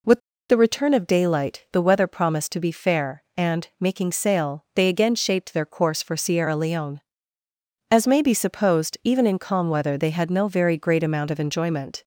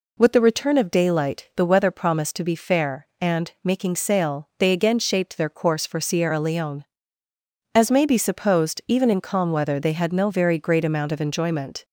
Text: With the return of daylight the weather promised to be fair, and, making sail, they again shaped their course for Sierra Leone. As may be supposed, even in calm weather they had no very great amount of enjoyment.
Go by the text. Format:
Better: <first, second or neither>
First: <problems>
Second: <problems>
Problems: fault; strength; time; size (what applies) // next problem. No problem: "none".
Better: second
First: pauses between "With" and "the"; slight; at 0.1 s; 0.31 s long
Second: none